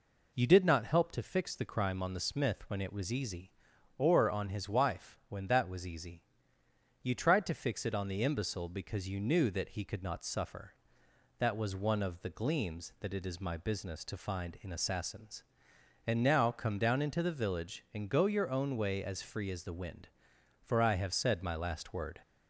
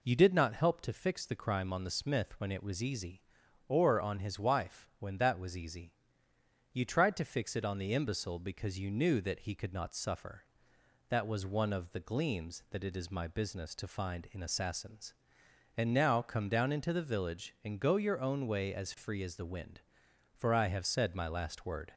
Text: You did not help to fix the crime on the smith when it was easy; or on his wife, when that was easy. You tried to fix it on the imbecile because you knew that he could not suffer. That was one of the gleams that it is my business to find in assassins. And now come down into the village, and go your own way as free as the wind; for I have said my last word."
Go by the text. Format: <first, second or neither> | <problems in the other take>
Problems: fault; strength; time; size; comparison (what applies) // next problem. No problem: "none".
neither | none